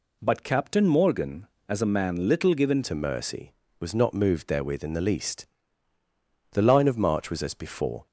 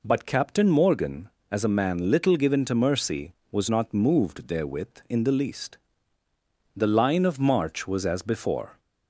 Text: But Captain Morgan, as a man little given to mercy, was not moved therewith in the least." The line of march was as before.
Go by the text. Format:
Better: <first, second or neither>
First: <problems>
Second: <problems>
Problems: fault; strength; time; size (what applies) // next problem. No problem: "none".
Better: second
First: changes voice at "to"; from 2.8 s on; 5.2 s long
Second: none